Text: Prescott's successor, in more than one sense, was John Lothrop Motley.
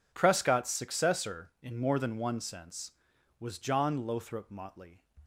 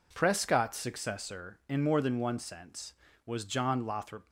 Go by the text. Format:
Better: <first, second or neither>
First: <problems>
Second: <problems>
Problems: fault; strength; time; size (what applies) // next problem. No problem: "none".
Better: first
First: none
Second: stops before "Motley"; at 4.2 s